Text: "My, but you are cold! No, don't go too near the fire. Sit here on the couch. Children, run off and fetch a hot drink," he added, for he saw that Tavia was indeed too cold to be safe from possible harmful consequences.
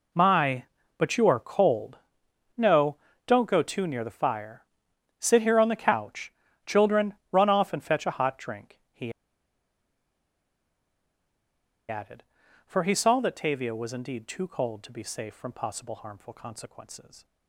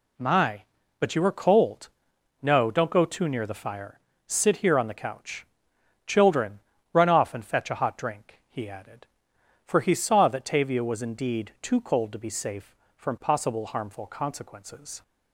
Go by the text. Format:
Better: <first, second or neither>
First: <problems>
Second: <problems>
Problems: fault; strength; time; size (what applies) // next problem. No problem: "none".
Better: second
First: pauses between "he" and "added"; strong; at 9.1 s; 2.7 s long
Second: none